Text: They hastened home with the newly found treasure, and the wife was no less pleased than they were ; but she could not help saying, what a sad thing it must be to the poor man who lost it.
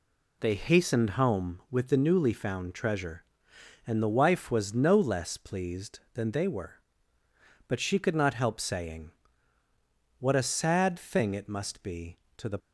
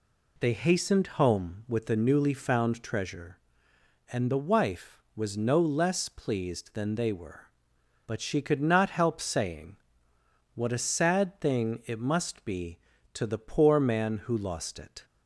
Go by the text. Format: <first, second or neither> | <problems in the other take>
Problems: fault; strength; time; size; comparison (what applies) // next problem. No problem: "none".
second | stops before "poor man who lost it"; at 12.5 s